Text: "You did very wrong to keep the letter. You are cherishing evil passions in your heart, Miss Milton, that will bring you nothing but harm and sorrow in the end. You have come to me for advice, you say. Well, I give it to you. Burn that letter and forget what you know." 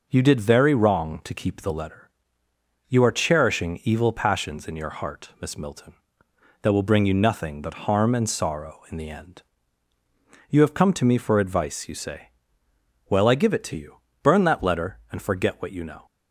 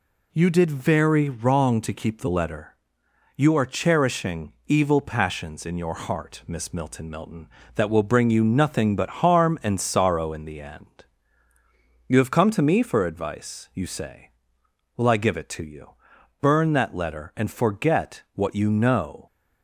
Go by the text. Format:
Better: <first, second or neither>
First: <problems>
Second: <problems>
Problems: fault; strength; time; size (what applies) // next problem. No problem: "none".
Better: first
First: none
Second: says "Milton" twice; at 7.0 s